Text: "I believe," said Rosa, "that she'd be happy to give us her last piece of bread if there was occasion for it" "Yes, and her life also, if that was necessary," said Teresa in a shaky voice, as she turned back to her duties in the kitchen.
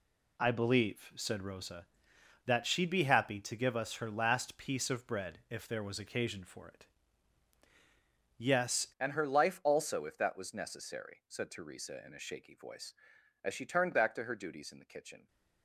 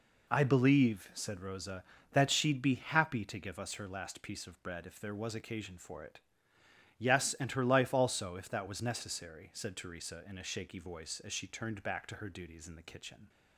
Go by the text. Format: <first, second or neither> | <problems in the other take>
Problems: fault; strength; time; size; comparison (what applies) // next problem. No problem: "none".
second | pauses between "it" and "Yes"; strong; at 6.8 s; 1.5 s long; noticeable in the second // changes voice at "and"; from 9.0 s on; 6.2 s long